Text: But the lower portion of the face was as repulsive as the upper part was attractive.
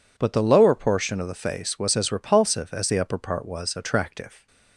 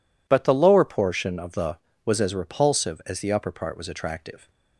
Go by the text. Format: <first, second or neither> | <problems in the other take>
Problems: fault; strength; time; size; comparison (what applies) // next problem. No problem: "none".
first | skips "face"; at 1.9 s